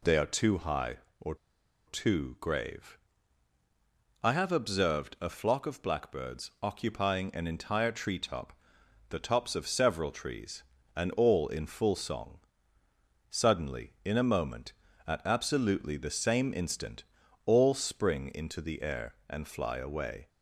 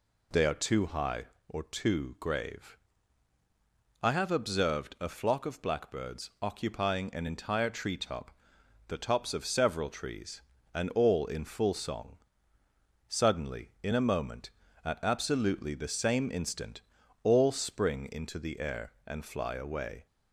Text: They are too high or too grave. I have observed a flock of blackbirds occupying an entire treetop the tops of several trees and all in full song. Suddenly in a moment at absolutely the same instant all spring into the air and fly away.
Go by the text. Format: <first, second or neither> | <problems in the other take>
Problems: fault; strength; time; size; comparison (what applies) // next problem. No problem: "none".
second | pauses between "or" and "too"; noticeable; at 1.3 s; 0.51 s long // pauses between "treetop" and "the"; noticeable; at 8.5 s; 0.56 s long; noticeable in the second // pauses between "instant" and "all"; at 17.0 s; 0.44 s long; also in the second